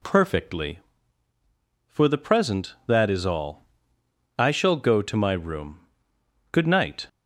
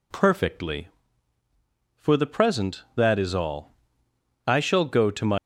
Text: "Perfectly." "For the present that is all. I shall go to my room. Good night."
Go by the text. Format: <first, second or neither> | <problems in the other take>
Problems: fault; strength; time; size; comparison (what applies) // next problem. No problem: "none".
first | stops before "room Good night"; at 5.3 s